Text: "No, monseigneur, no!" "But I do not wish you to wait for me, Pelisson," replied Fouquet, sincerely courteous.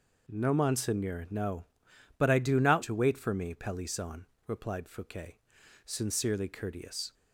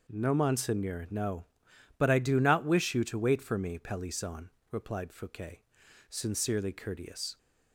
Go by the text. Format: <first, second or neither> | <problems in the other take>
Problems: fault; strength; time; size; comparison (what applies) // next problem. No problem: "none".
second | skips "wish you"; at 2.8 s